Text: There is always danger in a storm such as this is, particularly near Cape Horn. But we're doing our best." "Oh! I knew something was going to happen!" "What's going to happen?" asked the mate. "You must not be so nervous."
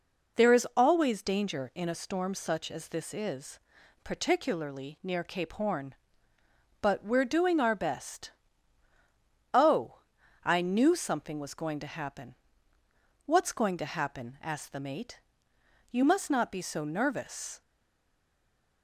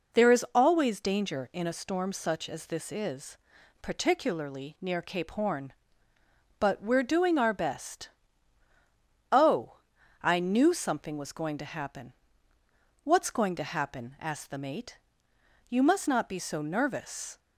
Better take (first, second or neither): second